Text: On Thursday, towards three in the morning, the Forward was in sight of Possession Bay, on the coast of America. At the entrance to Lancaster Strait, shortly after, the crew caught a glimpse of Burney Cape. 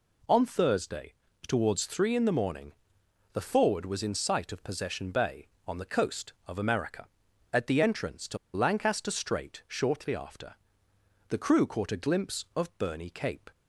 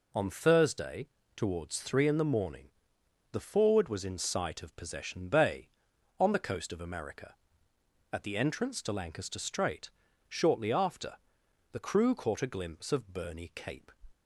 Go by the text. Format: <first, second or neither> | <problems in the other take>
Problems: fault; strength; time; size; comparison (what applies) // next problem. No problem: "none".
second | pauses between "to" and "Lancaster"; slight; at 8.3 s; 0.17 s long